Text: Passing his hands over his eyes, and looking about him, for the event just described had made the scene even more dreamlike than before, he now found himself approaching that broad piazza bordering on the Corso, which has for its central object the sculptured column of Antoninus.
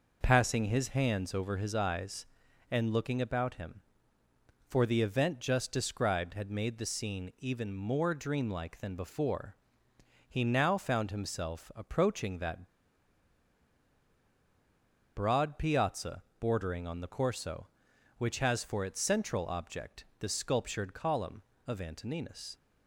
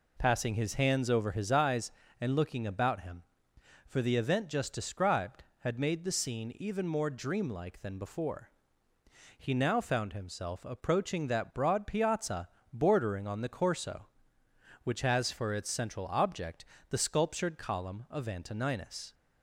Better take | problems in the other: second | pauses between "that" and "broad"; strong; at 12.6 s; 2.4 s long // pauses between "piazza" and "bordering"; slight; at 16.2 s; 0.16 s long; slight in the second // pauses between "object" and "the"; slight; at 20.0 s; 0.16 s long; slight in the second

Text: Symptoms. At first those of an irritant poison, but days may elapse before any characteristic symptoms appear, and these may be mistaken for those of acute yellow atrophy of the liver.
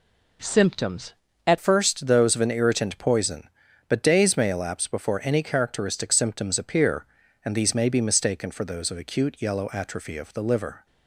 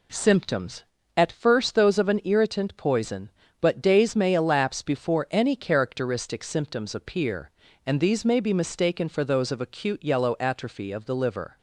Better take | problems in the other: second | changes voice at "first"; from 1.5 s on; 9.3 s long

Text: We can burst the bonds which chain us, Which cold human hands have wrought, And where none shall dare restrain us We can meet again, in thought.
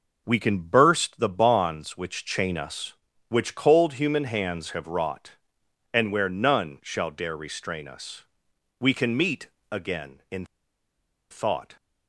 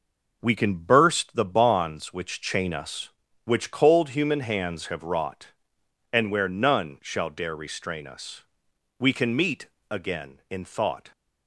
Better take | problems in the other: second | pauses between "us" and "We"; noticeable; at 8.2 s; 0.56 s long; noticeable in the second // pauses between "meet" and "again"; slight; at 9.4 s; 0.22 s long; slight in the second // pauses between "in" and "thought"; noticeable; at 10.4 s; 0.84 s long

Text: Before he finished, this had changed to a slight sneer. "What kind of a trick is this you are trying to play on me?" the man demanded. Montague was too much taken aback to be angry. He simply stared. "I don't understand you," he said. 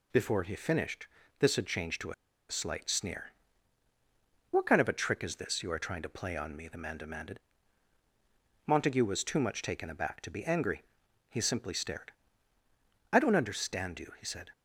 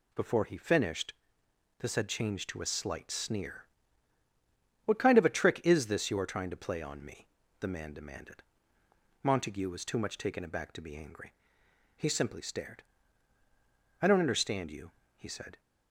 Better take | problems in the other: second | pauses between "a" and "slight"; at 2.1 s; 0.36 s long

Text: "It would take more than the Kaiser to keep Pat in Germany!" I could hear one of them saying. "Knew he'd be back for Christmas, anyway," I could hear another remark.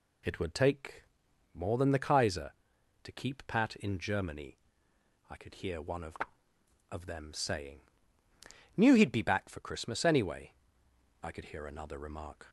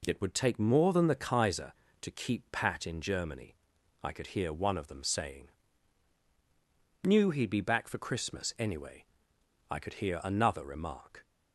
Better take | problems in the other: second | pauses between "take" and "more"; noticeable; at 1.0 s; 0.50 s long // says "of" twice; at 6.9 s

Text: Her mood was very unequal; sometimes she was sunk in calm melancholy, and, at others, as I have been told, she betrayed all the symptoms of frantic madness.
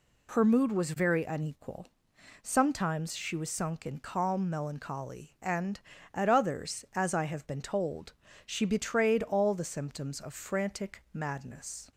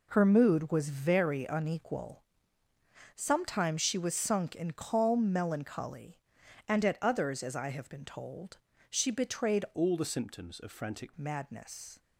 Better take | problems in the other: first | changes voice from "all" to "frantic"; from 9.7 to 11.1 s; 1.4 s long

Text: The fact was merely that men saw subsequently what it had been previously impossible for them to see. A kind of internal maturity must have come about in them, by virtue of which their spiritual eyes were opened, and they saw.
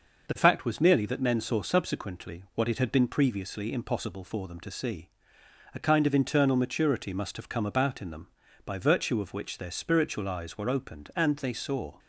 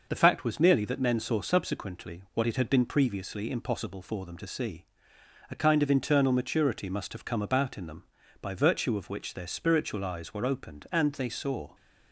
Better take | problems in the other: neither | none

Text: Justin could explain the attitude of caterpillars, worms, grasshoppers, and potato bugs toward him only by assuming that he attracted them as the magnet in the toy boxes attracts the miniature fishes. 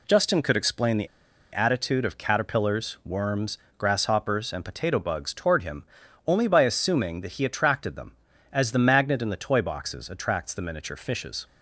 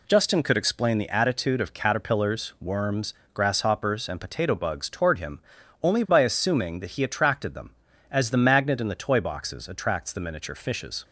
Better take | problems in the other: second | pauses between "the" and "attitude"; at 1.0 s; 0.45 s long // pauses between "him" and "only"; at 5.8 s; 0.42 s long; also in the second

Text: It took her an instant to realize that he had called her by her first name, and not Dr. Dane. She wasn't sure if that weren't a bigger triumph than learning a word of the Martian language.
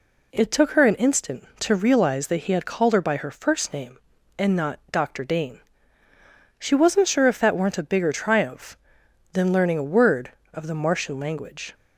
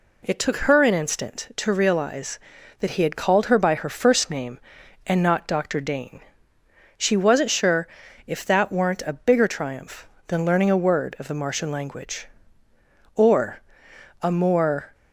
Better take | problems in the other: first | pauses between "sure" and "if"; at 7.8 s; 0.40 s long // goes on to say "Or a more"; strong; from 13.1 s on; 1.7 s long

